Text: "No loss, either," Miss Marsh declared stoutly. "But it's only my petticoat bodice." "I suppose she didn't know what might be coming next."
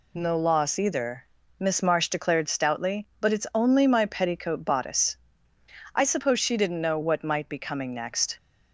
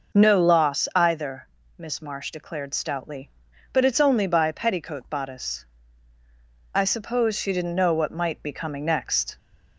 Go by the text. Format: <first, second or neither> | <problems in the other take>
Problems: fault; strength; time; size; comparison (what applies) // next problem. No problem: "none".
first | says "by" for "my"; at 4.2 s